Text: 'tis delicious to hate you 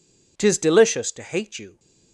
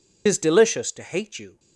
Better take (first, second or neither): first